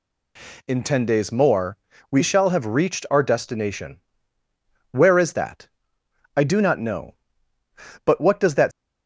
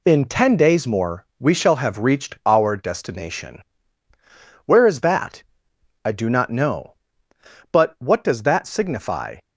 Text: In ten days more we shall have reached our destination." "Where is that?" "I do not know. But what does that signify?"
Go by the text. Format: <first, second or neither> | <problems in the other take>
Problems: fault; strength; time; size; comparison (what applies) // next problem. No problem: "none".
second | pauses between "more" and "we"; slight; at 1.7 s; 0.32 s long // stops before "signify"; at 8.7 s